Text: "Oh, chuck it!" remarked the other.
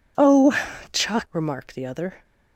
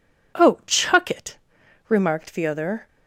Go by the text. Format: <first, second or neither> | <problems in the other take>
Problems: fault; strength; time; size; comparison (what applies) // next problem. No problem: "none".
second | skips "it"; at 1.2 s